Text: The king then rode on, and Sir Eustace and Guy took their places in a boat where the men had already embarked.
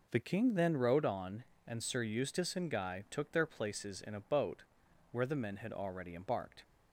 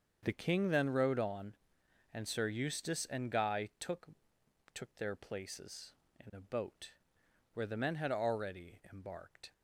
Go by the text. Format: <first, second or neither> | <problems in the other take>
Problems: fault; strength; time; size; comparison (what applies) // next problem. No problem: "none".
first | starts louder than the rest; until 1.2 s; 6.5 dB // says "took" twice; at 4.7 s // pauses between "boat" and "where"; noticeable; at 6.9 s; 0.64 s long; noticeable in the first